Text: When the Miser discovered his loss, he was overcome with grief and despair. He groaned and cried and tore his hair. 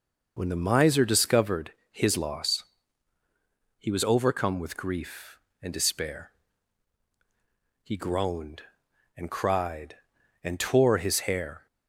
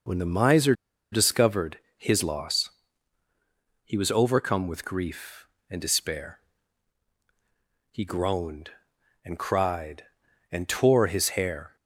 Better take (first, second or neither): first